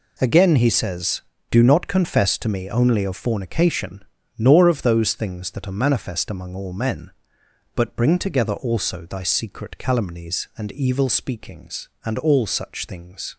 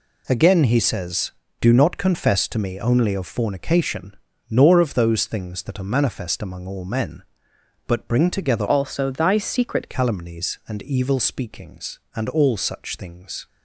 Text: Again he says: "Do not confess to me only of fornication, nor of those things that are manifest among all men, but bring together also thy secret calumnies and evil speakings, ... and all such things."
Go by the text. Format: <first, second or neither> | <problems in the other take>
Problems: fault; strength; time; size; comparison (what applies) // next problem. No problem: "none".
first | changes voice from "also" to "secret"; from 8.6 to 9.8 s; 1.2 s long